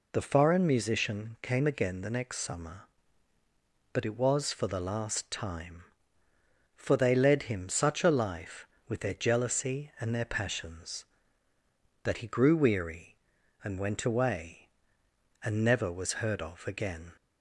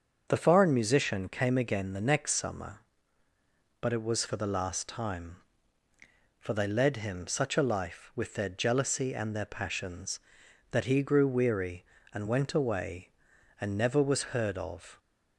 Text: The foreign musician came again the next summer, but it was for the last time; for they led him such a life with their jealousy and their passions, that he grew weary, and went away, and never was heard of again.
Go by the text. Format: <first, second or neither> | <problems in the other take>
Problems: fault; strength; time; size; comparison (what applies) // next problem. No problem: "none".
first | starts louder than the rest; until 1.2 s; 6.5 dB // stops before "again"; at 14.9 s